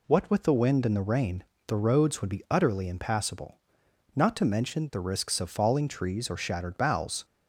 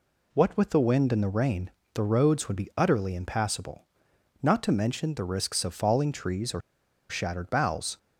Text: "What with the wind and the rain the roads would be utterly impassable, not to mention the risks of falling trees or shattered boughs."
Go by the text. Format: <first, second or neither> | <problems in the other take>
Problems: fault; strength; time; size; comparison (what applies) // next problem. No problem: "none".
first | pauses between "rain" and "the"; slight; at 1.7 s; 0.24 s long; slight in the first // pauses between "or" and "shattered"; noticeable; at 6.6 s; 0.48 s long